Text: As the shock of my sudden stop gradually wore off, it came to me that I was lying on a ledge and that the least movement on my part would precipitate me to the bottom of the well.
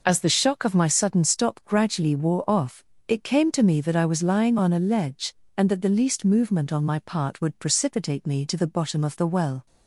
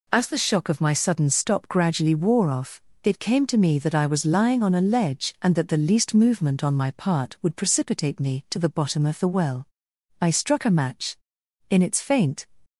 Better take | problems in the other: first | goes on to say "I struck a match In its faint"; strong; from 10.2 s on; 2.2 s long

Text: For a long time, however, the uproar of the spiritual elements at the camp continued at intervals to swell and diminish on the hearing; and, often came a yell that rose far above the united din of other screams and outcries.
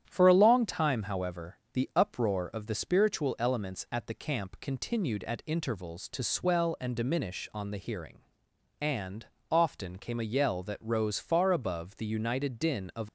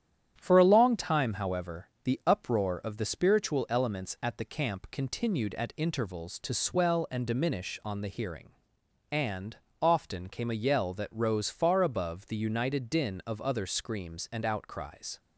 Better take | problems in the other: second | starts louder than the rest; strong; until 1.1 s; 10 dB; strong in the second // stops before "other screams and outcries"; at 13.0 s

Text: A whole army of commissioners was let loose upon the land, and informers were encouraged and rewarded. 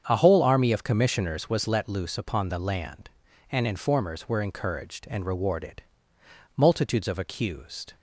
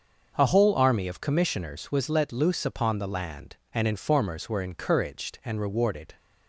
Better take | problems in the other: second | starts louder than the rest; strong; until 1.0 s; 7.5 dB; also in the second // goes on to say "Multitudes of accused"; from 6.5 s on; 1.4 s long

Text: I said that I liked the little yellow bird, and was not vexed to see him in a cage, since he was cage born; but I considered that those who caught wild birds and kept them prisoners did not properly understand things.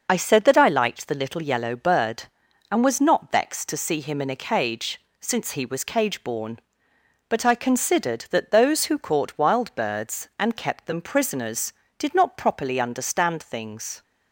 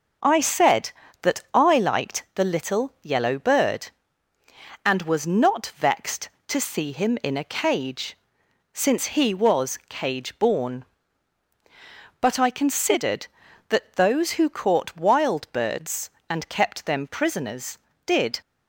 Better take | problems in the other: first | starts louder than the rest; until 1.6 s; 6.5 dB // stops before "not properly understand things"; at 18.4 s

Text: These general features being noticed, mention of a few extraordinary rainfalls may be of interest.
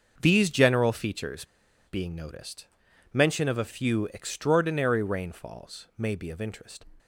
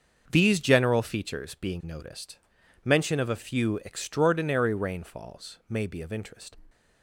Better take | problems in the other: second | starts louder than the rest; until 1.2 s; 6.5 dB; also in the second // pauses between "features" and "being"; at 1.4 s; 0.43 s long

